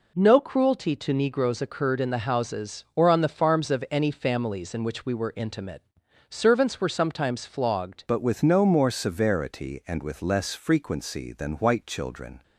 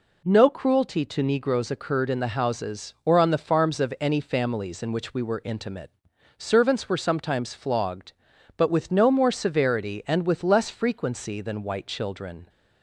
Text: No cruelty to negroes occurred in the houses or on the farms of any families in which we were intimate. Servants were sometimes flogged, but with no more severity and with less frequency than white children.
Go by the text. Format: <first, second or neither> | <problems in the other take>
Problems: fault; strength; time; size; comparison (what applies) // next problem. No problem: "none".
second | changes voice at "but"; from 8.0 s on; 4.4 s long